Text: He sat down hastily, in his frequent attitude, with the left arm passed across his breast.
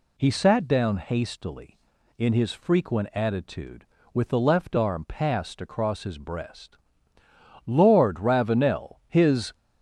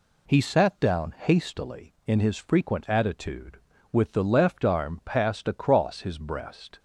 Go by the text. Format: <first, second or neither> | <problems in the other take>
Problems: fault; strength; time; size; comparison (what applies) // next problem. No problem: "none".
second | goes on to say "Lord Ravenel His"; strong; from 7.6 s on; 1.8 s long